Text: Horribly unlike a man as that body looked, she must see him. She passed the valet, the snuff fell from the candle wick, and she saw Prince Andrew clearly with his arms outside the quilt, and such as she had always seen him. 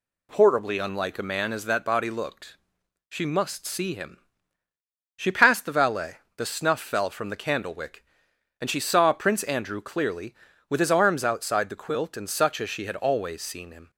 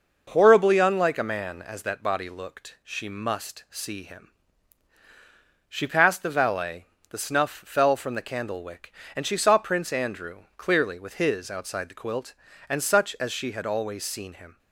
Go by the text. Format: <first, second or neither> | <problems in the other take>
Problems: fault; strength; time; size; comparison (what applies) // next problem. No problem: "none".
first | pauses between "Andrew" and "clearly"; slight; at 10.4 s; 0.18 s long // skips "arms"; at 11.5 s